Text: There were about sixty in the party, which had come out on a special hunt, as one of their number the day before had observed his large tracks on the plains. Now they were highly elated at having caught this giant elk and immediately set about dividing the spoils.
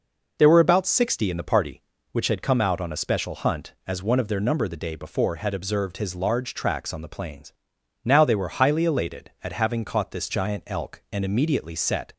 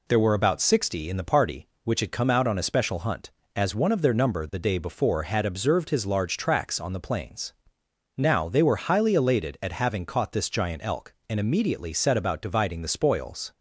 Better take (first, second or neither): second